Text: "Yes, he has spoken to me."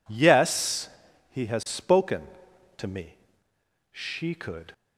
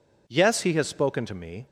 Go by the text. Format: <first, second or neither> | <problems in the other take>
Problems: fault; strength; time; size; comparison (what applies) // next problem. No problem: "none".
second | goes on to say "She could"; noticeable; from 3.9 s on; 0.82 s long